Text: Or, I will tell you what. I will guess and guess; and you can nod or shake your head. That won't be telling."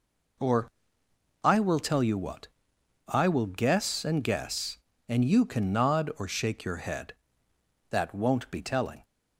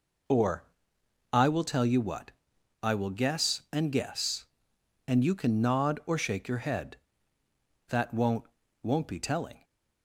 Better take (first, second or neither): first